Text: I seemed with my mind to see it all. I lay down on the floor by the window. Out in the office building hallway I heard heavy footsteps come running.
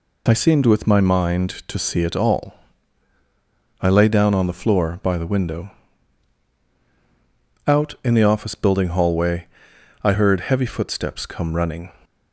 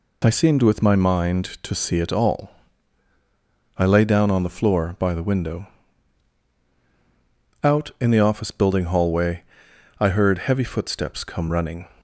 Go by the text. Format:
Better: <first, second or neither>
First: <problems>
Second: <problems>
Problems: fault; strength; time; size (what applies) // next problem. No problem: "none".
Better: neither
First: pauses between "hallway" and "I"; noticeable; at 9.4 s; 0.56 s long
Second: pauses between "hallway" and "I"; noticeable; at 9.4 s; 0.56 s long